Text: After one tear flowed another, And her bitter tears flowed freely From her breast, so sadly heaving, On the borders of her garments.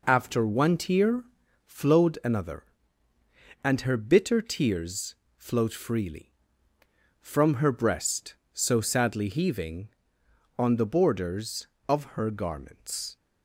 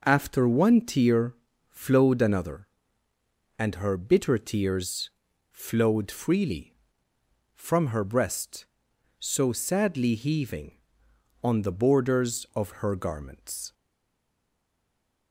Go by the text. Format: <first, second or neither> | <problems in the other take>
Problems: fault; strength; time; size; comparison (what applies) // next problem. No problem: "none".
first | pauses between "tear" and "flowed"; slight; at 1.3 s; 0.36 s long; also in the first // pauses between "tears" and "flowed"; at 5.0 s; 0.44 s long; slight in the first // stays silent after the last word; noticeable; from 13.7 s on; 1.6 s long